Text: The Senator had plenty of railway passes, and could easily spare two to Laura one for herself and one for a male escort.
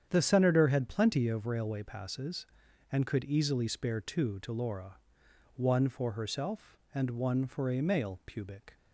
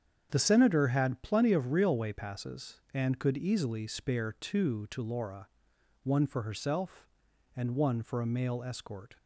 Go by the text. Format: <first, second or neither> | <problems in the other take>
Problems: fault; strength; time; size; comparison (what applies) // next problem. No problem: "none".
second | starts louder than the rest; strong; until 1.1 s; 8.5 dB; strong in the second // pauses between "Laura" and "one"; noticeable; at 4.9 s; 0.58 s long; noticeable in the second // says "pubic" for "escort"; at 8.2 s